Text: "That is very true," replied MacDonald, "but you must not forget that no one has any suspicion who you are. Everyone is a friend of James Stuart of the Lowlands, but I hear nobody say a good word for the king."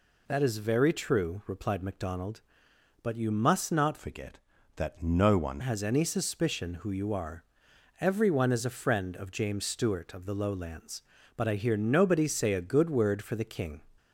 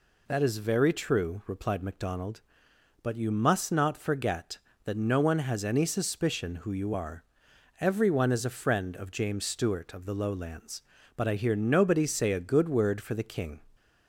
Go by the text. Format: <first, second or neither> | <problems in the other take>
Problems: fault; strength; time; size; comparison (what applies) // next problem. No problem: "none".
second | changes voice from "forget" to "one"; from 3.9 to 5.6 s; 1.7 s long